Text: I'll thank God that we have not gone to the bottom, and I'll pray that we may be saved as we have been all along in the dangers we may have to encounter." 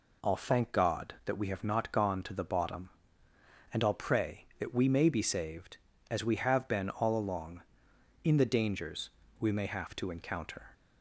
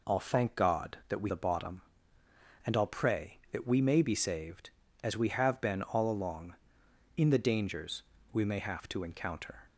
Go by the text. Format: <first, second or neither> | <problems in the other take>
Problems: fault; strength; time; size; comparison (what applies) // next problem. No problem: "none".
first | skips "have not gone to"; at 1.2 s // pauses between "dangers" and "we"; slight; at 8.0 s; 0.32 s long; slight in the first